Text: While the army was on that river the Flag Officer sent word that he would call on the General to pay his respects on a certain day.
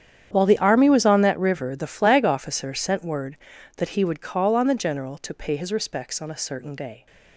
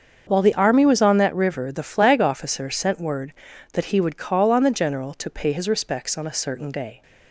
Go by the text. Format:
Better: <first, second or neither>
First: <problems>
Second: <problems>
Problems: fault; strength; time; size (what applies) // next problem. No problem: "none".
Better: second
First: gets quieter; strong; throughout; 17 dB // starts louder than the rest; strong; until 1.3 s; 9 dB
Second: starts louder than the rest; until 1.3 s; 7 dB